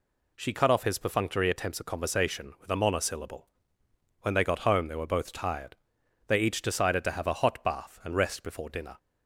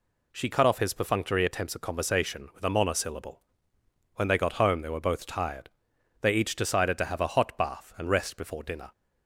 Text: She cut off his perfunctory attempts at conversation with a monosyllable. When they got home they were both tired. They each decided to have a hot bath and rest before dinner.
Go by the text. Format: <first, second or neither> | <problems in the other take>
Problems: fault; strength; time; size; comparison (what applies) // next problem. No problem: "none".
neither | none